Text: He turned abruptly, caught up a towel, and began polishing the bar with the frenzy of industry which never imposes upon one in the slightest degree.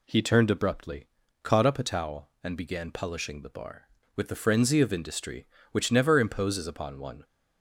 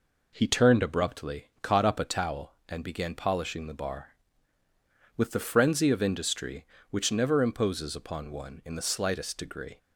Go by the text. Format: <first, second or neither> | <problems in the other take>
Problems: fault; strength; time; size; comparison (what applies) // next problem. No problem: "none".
second | stops before "in the slightest degree"; at 7.2 s